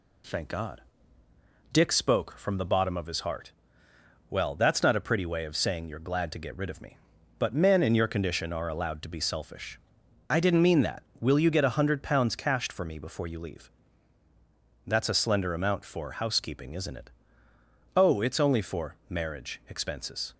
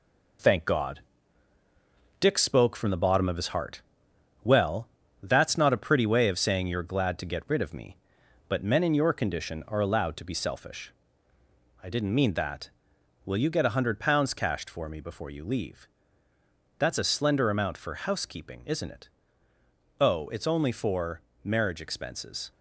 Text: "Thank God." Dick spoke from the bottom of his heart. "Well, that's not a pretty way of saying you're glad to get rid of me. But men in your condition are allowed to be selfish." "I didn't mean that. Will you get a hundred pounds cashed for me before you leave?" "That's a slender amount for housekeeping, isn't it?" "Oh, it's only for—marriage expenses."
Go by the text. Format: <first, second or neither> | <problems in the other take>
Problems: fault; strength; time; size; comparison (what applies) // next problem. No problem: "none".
first | gets quieter; noticeable; throughout; 5 dB